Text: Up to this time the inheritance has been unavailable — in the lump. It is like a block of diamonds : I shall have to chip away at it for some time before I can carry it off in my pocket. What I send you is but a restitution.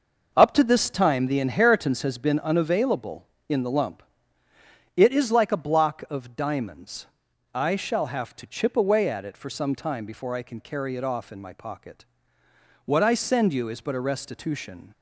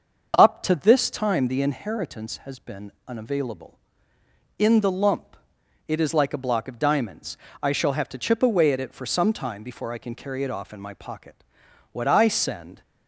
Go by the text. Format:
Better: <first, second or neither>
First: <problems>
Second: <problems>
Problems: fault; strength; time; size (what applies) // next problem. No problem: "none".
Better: first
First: none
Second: starts louder than the rest; until 1.3 s; 6.5 dB // pauses between "been" and "unavailable"; slight; at 2.9 s; 0.16 s long // stops before "you is but a restitution"; at 12.8 s